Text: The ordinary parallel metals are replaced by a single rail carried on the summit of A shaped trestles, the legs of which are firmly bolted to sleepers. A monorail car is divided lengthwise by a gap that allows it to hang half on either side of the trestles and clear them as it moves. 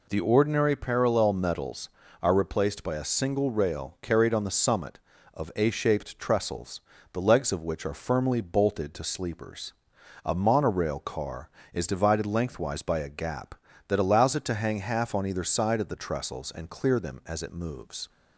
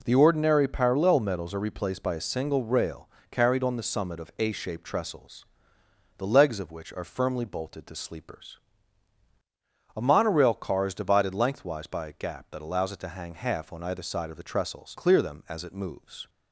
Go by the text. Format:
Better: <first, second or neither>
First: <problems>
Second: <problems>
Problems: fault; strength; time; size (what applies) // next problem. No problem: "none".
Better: first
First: none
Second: pauses between "rail" and "carried"; slight; at 3.0 s; 0.22 s long // skips "and"; at 14.9 s